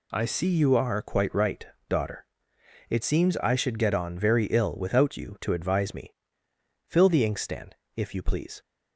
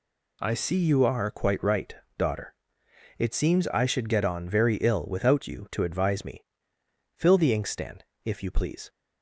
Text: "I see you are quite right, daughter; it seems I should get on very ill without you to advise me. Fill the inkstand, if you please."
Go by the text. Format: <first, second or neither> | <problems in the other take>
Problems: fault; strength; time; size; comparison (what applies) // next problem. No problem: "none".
neither | none